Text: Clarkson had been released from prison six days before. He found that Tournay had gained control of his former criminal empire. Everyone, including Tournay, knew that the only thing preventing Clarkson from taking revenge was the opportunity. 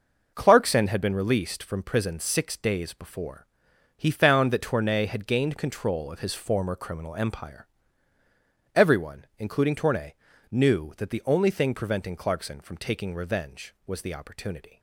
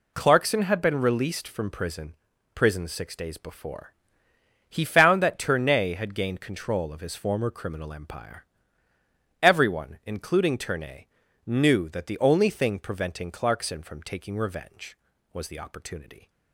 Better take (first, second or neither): first